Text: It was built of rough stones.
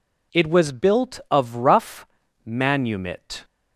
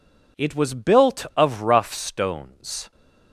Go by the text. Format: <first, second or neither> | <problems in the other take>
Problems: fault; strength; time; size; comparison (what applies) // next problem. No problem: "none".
second | says "manumit" for "stones"; at 2.4 s